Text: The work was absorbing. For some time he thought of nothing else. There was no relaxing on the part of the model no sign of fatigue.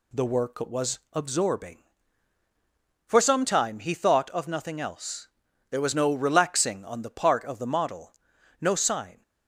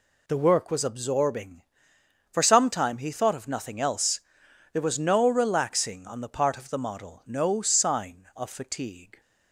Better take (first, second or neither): second